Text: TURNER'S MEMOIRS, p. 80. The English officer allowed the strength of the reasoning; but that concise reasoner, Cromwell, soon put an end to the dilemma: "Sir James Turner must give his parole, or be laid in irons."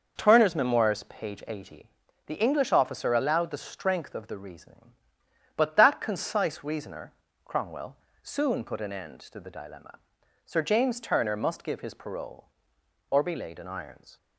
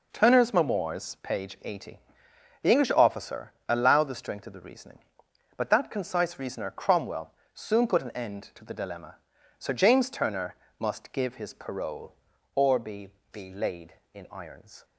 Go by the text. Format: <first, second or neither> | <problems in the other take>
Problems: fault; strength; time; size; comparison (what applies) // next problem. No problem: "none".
first | pauses between "officer" and "allowed"; slight; at 3.5 s; 0.16 s long // pauses between "Turner" and "must"; slight; at 10.5 s; 0.24 s long // says "be" twice; at 13.3 s